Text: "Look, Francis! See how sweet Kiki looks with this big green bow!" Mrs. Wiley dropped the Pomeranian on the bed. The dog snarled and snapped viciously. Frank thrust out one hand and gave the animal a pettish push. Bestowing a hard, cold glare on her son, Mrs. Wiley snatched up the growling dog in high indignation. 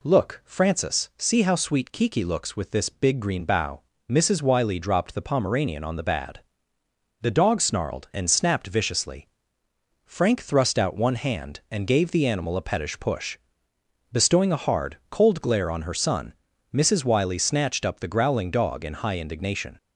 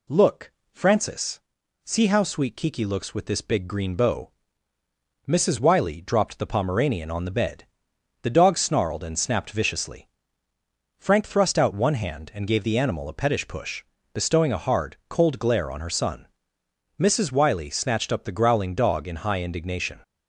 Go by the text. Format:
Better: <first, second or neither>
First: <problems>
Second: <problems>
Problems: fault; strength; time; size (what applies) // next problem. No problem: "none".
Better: second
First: says "bad" for "bed"; at 6.0 s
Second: none